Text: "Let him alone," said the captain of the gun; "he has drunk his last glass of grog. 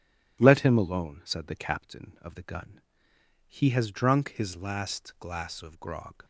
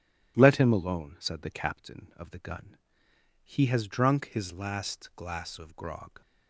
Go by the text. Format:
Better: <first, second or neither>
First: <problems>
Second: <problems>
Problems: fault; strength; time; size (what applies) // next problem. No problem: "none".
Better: neither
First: starts louder than the rest; strong; until 1.4 s; 11.5 dB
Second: starts louder than the rest; strong; until 1.3 s; 11.5 dB